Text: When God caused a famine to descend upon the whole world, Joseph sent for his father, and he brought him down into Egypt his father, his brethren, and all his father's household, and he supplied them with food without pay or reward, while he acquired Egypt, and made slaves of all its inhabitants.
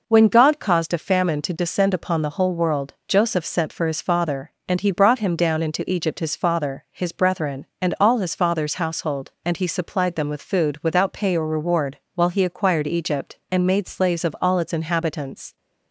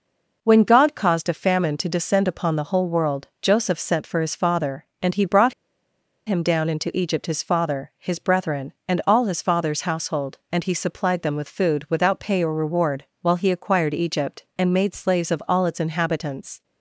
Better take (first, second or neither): first